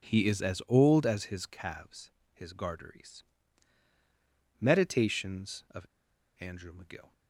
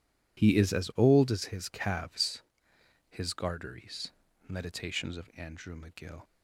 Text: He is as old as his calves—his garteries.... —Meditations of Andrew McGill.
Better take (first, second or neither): second